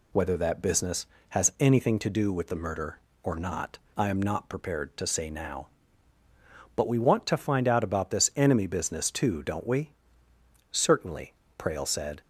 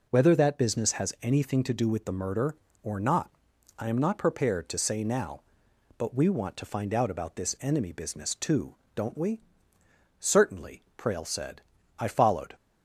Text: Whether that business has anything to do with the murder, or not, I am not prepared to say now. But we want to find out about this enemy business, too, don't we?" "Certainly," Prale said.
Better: first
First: none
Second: goes on to say "I followed"; from 11.9 s on; 0.56 s long

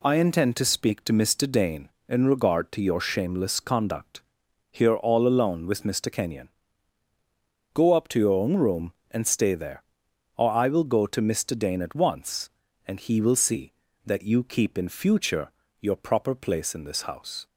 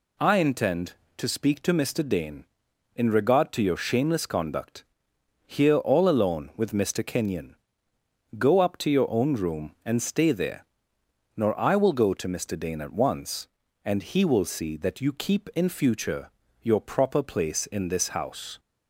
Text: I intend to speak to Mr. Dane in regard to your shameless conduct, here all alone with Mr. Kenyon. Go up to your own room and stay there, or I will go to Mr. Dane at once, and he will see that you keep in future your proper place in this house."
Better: first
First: pauses between "future" and "your"; slight; at 15.5 s; 0.28 s long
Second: says "nor" for "or"; at 11.3 s // pauses between "future" and "your"; slight; at 16.2 s; 0.32 s long

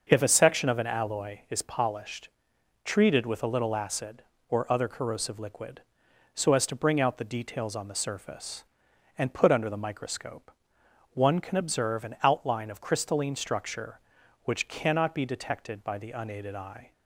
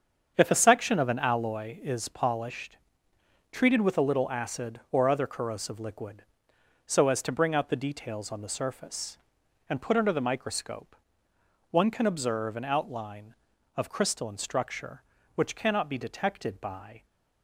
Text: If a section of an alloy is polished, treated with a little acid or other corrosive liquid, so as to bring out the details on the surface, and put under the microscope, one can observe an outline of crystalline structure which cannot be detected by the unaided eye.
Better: first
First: starts louder than the rest; until 1.1 s; 6.5 dB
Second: starts louder than the rest; strong; until 1.3 s; 7.5 dB // stops before "the unaided eye"; at 17.0 s

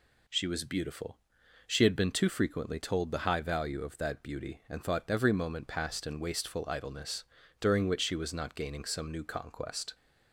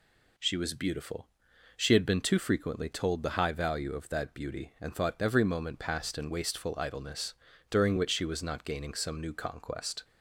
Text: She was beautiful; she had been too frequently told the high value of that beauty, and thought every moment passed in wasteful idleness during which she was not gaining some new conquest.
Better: neither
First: pauses between "idleness" and "during"; slight; at 7.2 s; 0.34 s long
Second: pauses between "idleness" and "during"; slight; at 7.3 s; 0.34 s long

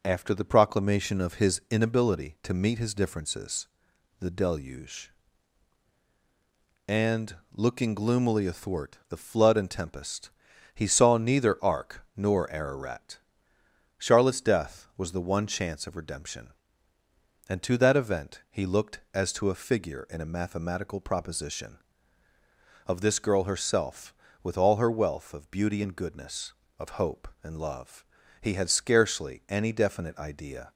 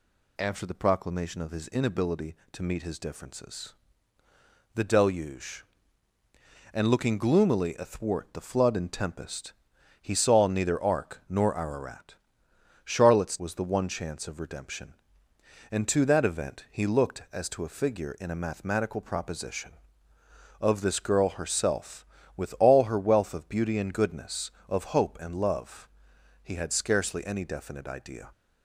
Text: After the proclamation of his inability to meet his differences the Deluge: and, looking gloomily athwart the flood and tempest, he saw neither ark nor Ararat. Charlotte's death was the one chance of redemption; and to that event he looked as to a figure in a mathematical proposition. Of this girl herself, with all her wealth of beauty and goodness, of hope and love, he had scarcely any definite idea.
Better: first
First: pauses between "differences" and "the"; noticeable; at 3.6 s; 0.54 s long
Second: pauses between "differences" and "the"; at 3.7 s; 1.0 s long // skips "death"; at 13.3 s

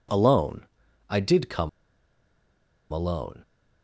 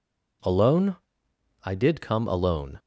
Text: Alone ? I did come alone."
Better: second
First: pauses between "come" and "alone"; at 1.6 s; 1.2 s long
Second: none

